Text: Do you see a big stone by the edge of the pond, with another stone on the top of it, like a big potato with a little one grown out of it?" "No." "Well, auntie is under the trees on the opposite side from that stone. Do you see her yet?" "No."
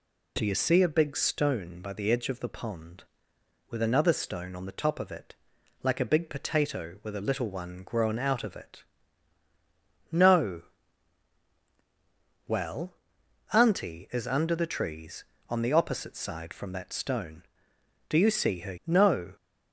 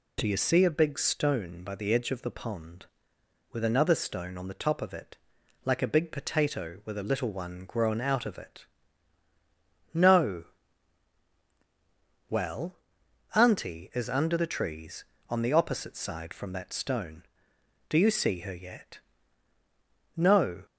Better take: second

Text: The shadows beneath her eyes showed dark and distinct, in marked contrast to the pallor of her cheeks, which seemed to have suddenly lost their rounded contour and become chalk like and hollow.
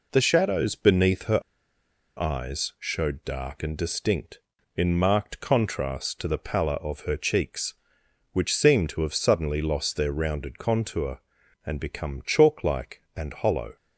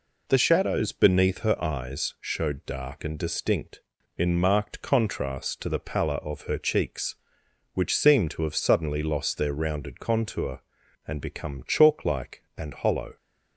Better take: second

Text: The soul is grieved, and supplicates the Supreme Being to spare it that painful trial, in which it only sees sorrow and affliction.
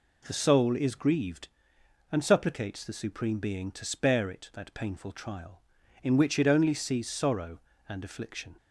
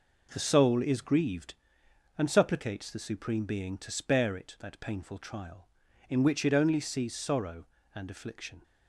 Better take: first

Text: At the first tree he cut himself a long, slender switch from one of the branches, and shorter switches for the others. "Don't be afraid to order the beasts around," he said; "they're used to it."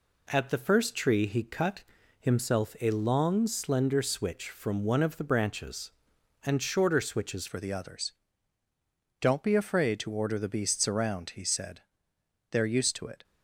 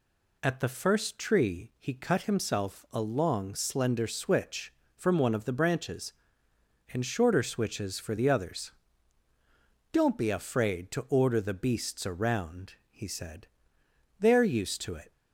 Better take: second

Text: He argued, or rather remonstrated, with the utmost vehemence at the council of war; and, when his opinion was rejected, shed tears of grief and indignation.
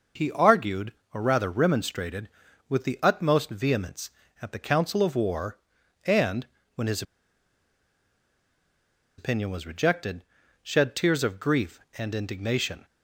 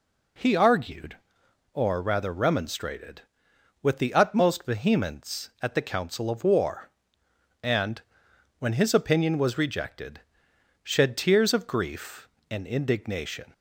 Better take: second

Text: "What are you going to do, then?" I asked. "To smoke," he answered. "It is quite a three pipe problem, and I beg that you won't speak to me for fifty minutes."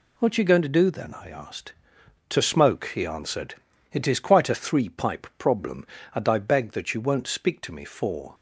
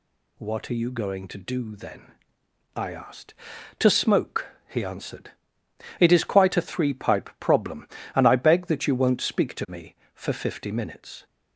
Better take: second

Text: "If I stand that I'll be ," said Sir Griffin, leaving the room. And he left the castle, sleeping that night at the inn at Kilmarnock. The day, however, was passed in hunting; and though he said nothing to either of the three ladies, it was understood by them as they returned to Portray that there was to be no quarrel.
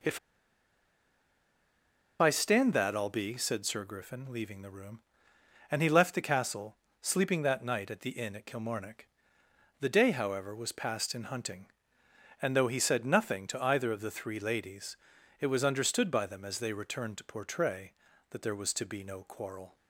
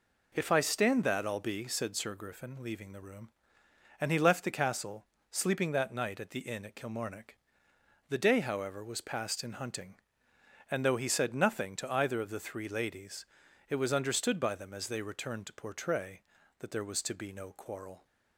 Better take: second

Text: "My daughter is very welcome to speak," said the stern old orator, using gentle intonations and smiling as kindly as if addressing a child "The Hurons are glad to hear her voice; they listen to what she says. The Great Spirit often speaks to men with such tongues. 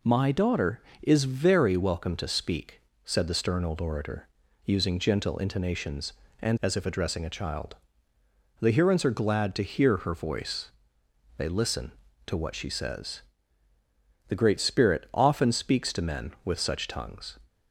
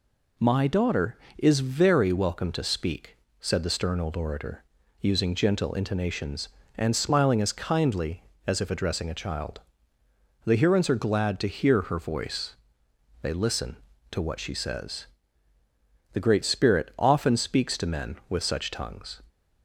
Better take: second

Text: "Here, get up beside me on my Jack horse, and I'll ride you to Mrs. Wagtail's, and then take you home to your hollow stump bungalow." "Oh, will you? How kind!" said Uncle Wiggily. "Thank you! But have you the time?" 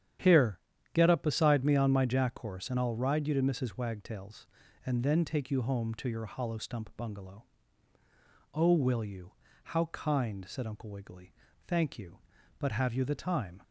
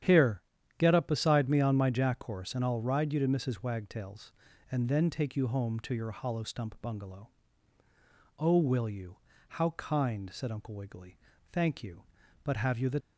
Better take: first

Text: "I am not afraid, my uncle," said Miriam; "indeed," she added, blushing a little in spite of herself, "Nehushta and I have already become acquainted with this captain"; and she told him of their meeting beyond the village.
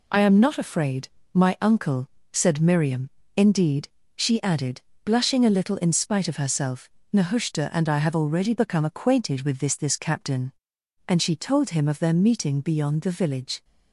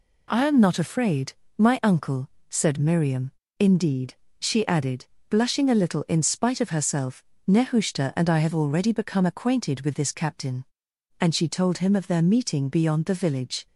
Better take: second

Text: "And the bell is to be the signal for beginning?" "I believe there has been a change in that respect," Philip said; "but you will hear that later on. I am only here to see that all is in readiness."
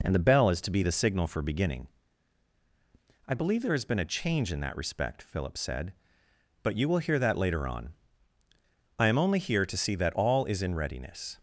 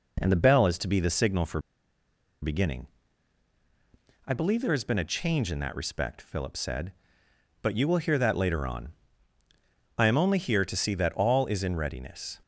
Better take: first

